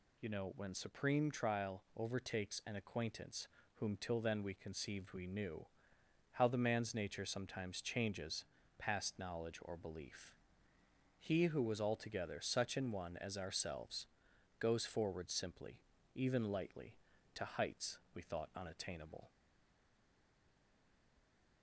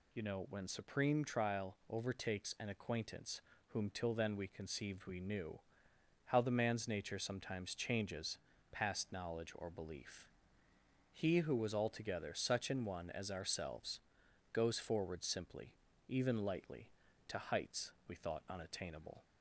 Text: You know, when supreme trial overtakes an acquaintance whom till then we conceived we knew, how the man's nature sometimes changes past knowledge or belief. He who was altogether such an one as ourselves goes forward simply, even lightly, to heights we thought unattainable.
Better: second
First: pauses between "acquaintance" and "whom"; slight; at 3.4 s; 0.30 s long // pauses between "changes" and "past"; slight; at 8.4 s; 0.36 s long // pauses between "ourselves" and "goes"; noticeable; at 14.0 s; 0.50 s long // pauses between "heights" and "we"; slight; at 17.9 s; 0.16 s long // stays silent after the last word; from 19.2 s on; 2.4 s long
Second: pauses between "acquaintance" and "whom"; slight; at 3.3 s; 0.30 s long // pauses between "changes" and "past"; slight; at 8.3 s; 0.36 s long // pauses between "ourselves" and "goes"; noticeable; at 14.0 s; 0.50 s long // pauses between "heights" and "we"; slight; at 17.9 s; 0.16 s long

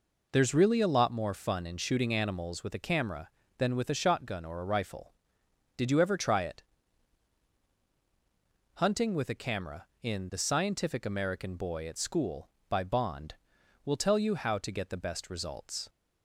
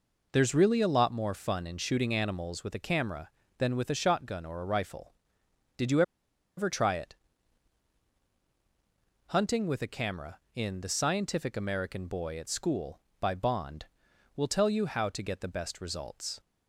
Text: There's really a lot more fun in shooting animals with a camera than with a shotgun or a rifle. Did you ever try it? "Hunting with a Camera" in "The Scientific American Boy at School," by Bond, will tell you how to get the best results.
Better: first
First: none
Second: pauses between "you" and "ever"; noticeable; at 6.0 s; 0.55 s long

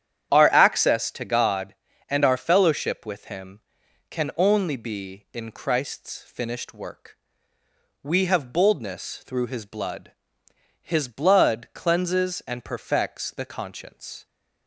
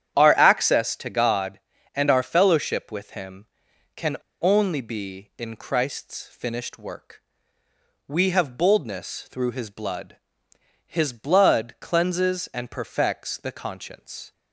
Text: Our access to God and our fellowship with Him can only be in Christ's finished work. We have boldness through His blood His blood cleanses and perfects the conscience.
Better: first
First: starts louder than the rest; strong; until 1.3 s; 9.5 dB // pauses between "blood" and "His"; noticeable; at 10.1 s; 0.72 s long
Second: starts louder than the rest; strong; until 1.2 s; 9.5 dB // pauses between "can" and "only"; slight; at 4.1 s; 0.27 s long // pauses between "blood" and "His"; noticeable; at 10.1 s; 0.72 s long

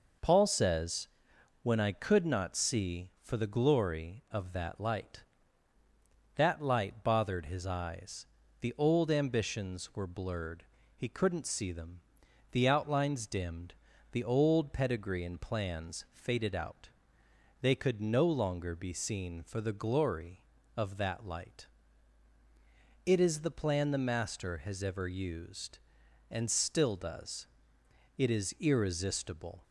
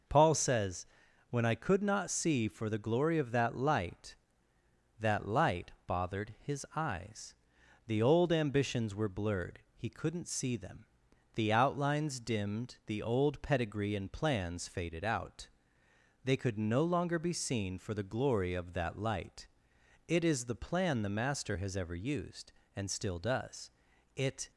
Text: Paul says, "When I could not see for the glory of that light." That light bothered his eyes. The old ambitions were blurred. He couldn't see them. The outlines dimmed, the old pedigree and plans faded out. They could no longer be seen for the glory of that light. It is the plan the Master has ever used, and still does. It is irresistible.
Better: first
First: none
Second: stops before "is irresistible"; at 24.5 s

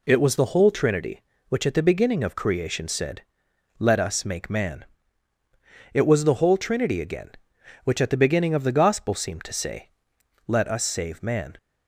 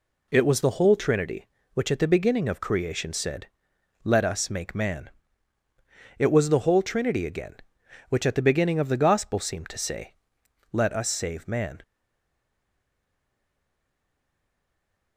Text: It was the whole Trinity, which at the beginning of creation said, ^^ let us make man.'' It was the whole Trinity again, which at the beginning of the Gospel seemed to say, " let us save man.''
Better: first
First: none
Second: stays silent after the last word; strong; from 11.8 s on; 3.3 s long

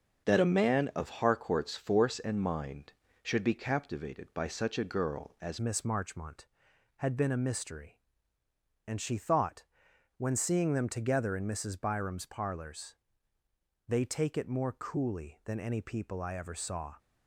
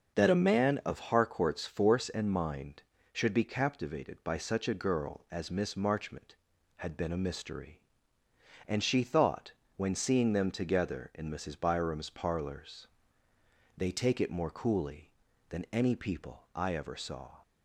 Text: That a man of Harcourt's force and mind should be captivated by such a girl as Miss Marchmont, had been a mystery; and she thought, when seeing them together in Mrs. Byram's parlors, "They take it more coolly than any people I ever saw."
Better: second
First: starts louder than the rest; until 1.3 s; 7 dB // changes voice at "Miss"; from 5.5 s on; 11.4 s long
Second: starts louder than the rest; until 1.2 s; 6.5 dB

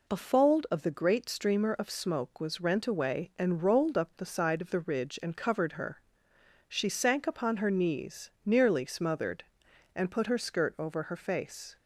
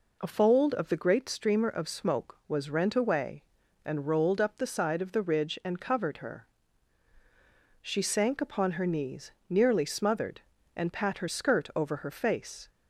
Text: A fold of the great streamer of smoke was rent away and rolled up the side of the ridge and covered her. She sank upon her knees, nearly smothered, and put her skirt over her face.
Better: first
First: none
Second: says "pat" for "put"; at 10.9 s

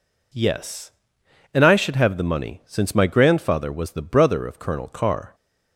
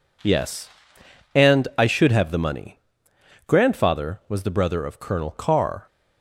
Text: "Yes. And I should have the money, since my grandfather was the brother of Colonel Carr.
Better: first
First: none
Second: skips "since my"; at 3.1 s

